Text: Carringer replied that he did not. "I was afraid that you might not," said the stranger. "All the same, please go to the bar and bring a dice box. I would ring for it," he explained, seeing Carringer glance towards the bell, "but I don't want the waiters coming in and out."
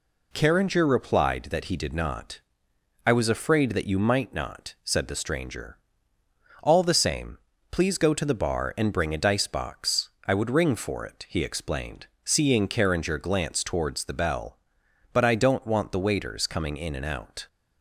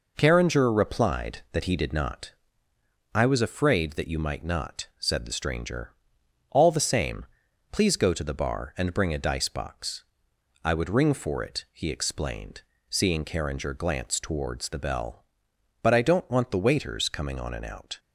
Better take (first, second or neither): first